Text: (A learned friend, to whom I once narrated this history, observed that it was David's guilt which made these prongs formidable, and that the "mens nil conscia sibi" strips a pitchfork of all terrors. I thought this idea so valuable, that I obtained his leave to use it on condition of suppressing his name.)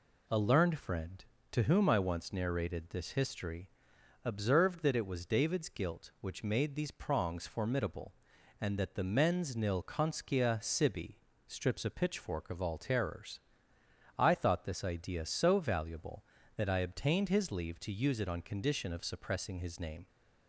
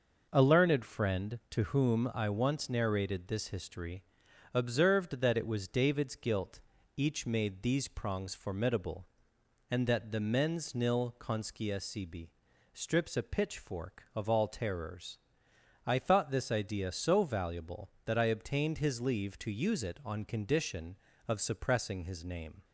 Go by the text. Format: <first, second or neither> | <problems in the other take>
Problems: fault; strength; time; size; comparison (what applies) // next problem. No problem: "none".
first | says "each" for "which"; at 6.9 s // pauses between "sibi" and "strips"; at 12.2 s; 0.44 s long; slight in the first